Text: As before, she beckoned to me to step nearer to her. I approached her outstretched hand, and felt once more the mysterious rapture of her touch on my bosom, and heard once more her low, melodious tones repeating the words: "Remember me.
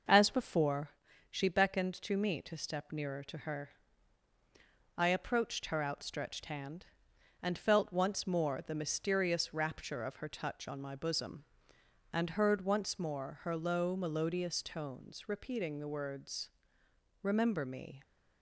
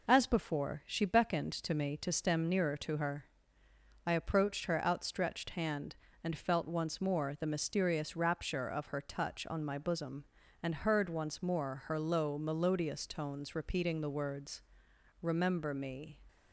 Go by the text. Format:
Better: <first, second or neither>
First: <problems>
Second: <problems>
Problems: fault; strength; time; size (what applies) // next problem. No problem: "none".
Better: first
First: none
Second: says "stem" for "step"; at 2.1 s